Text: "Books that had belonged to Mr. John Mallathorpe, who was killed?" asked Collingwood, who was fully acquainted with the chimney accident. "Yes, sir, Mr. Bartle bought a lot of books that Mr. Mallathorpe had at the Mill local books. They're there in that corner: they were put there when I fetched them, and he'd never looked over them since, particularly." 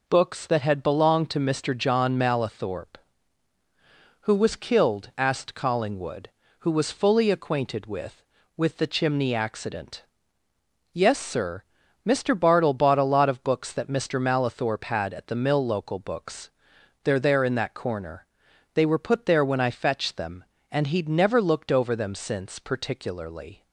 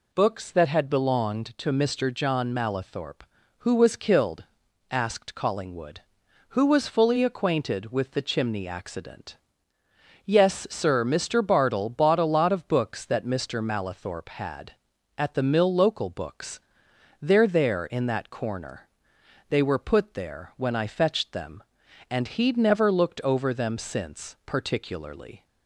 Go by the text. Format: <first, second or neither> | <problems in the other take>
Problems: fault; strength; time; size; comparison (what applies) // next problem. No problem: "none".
second | says "with" twice; at 8.5 s